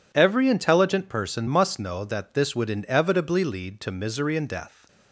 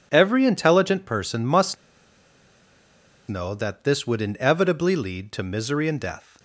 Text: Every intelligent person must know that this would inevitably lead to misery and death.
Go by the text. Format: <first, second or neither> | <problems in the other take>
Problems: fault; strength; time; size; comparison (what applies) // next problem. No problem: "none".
first | pauses between "must" and "know"; strong; at 1.7 s; 1.5 s long